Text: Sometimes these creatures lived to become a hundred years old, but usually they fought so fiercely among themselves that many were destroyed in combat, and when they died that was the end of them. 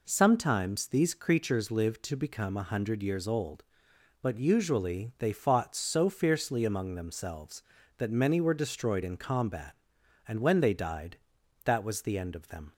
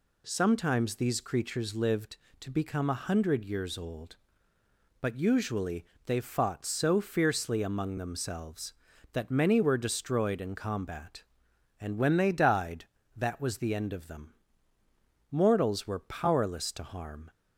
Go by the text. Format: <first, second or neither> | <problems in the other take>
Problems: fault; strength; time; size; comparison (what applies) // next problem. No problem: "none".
first | pauses between "usually" and "they"; slight; at 5.8 s; 0.22 s long // goes on to say "Mortals were powerless to harm"; strong; from 15.2 s on; 2.0 s long